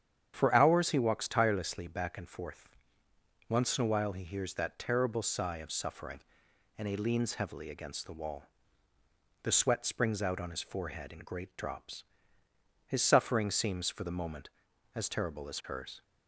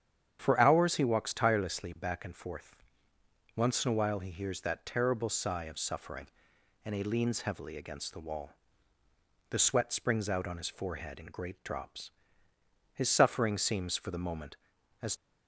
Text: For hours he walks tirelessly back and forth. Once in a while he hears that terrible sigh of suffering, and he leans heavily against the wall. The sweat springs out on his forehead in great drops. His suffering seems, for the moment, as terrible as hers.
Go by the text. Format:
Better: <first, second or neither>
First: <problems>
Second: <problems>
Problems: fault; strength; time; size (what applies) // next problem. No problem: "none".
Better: first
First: starts louder than the rest; strong; until 1.3 s; 8.5 dB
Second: starts louder than the rest; strong; until 1.4 s; 8.5 dB // stops before "terrible as hers"; at 15.1 s